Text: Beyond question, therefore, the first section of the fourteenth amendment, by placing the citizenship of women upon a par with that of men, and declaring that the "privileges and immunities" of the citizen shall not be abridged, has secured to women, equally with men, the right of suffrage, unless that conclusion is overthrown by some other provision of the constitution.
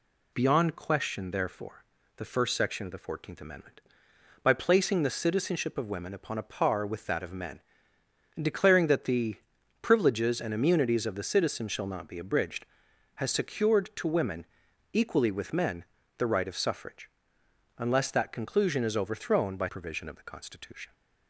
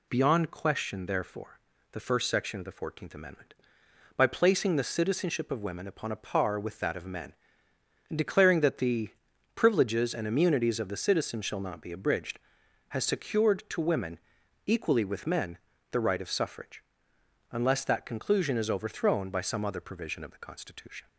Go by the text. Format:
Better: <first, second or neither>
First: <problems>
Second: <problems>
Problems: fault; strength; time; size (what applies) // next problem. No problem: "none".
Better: second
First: pauses between "the" and "privileges"; at 9.3 s; 0.44 s long // skips "some other"; at 19.6 s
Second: pauses between "the" and "privileges"; at 9.0 s; 0.44 s long